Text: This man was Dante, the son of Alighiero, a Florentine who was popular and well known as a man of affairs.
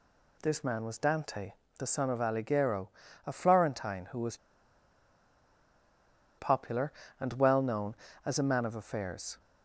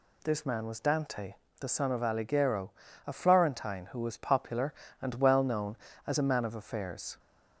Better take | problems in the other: second | pauses between "was" and "popular"; strong; at 4.3 s; 2.0 s long

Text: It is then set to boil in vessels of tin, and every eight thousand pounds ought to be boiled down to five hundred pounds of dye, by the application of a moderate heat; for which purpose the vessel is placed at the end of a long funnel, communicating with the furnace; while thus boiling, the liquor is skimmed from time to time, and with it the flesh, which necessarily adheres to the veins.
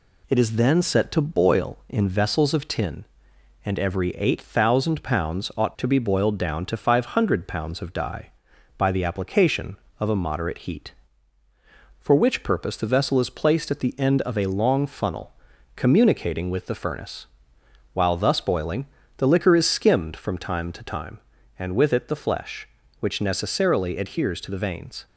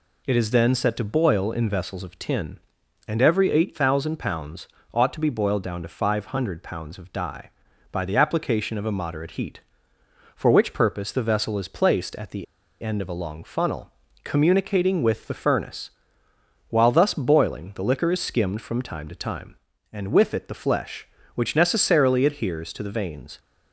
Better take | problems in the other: first | pauses between "pounds" and "ought"; slight; at 4.6 s; 0.26 s long // pauses between "the" and "end"; at 12.4 s; 0.37 s long

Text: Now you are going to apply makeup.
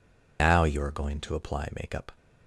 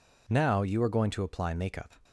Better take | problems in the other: second | loses the start of "Now"; at 0.3 s; 155 ms

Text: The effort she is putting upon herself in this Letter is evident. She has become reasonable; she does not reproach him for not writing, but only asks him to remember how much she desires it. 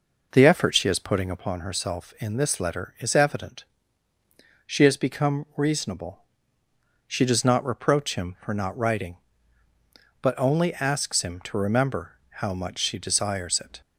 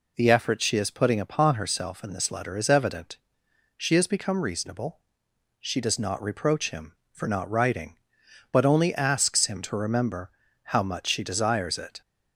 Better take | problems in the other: second | starts louder than the rest; noticeable; until 1.5 s; 5 dB // pauses between "remember" and "how"; slight; at 12.1 s; 0.22 s long; slight in the second

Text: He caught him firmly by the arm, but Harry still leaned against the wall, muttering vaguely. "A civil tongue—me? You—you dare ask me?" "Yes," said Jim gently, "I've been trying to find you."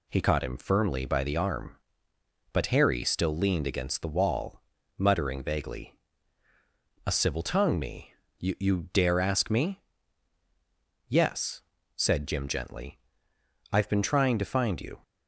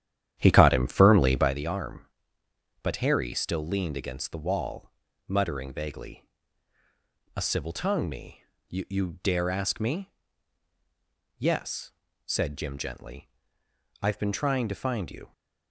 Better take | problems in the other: first | starts louder than the rest; strong; until 1.6 s; 10.5 dB

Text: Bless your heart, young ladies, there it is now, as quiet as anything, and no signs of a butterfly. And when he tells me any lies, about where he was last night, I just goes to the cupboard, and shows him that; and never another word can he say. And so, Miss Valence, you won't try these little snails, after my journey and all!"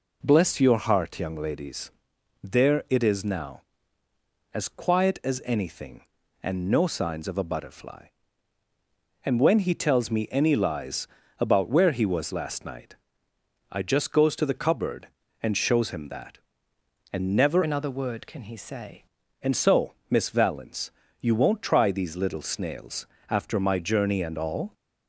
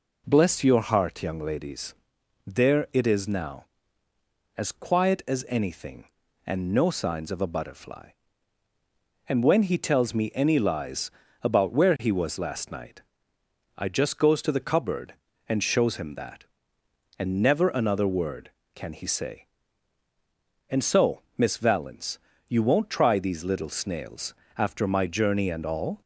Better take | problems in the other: second | changes voice from "another" to "say"; from 17.6 to 19.0 s; 1.4 s long

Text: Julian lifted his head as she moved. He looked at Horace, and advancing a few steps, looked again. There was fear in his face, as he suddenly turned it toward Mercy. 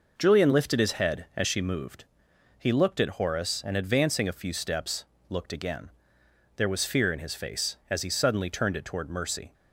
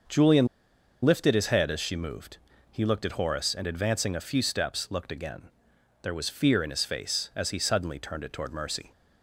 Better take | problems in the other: first | starts louder than the rest; until 1.6 s; 6.5 dB // pauses between "Julian" and "lifted"; noticeable; at 0.4 s; 0.57 s long

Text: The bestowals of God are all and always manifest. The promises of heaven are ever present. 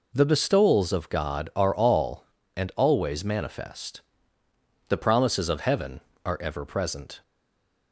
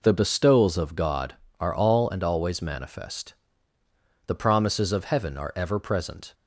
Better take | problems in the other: second | stays silent after the last word; slight; from 7.2 s on; 0.7 s long

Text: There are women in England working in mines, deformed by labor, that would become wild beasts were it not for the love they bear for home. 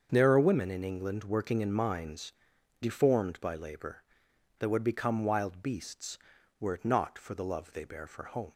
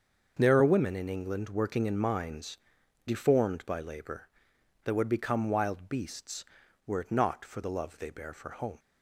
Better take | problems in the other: neither | starts louder than the rest; the same in both

